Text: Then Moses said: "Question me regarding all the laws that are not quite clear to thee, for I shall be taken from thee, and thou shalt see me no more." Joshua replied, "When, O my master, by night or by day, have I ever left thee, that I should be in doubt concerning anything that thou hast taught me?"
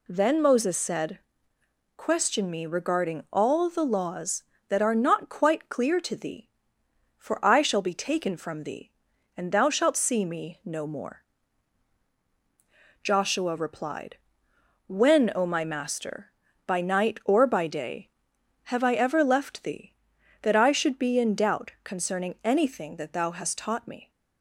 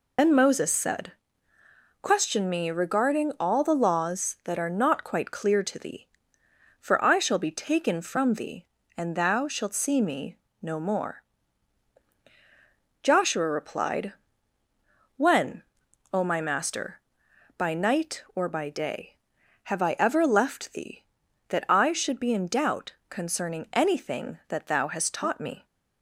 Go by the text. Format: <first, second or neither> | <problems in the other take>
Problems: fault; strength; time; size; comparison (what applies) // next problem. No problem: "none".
first | loses the start of "Then"; at 0.1 s; 115 ms // pauses between "me" and "no"; slight; at 10.3 s; 0.24 s long // pauses between "doubt" and "concerning"; slight; at 22.9 s; 0.16 s long